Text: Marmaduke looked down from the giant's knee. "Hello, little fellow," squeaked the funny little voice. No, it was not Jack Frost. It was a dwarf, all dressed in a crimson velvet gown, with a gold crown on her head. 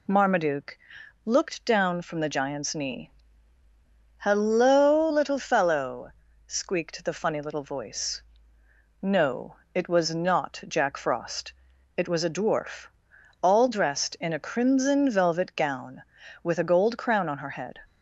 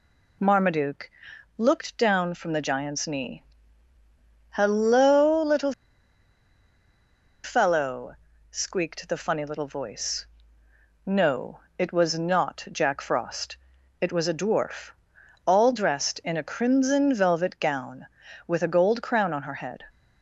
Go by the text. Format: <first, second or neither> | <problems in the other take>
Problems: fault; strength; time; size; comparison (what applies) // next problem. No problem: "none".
first | pauses between "Marmaduke" and "looked"; noticeable; at 1.1 s; 0.46 s long; noticeable in the first // pauses between "little" and "fellow"; strong; at 5.7 s; 1.7 s long